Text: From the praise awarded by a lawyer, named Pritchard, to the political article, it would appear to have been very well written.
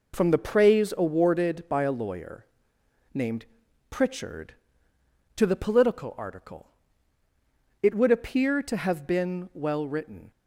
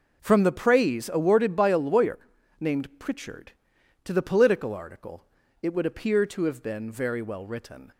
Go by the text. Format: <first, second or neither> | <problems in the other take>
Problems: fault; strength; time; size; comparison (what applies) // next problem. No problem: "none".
second | pauses between "named" and "Pritchard"; at 3.4 s; 0.44 s long // skips "very"; at 9.5 s